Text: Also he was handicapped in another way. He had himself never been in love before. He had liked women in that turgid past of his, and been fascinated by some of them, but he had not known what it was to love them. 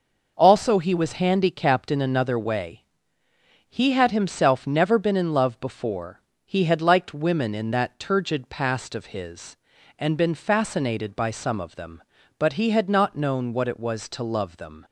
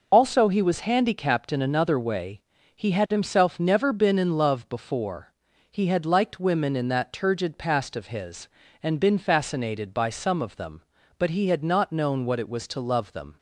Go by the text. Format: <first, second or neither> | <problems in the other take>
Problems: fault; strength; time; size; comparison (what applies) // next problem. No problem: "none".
first | loses the start of "Also"; at 0.1 s; 65 ms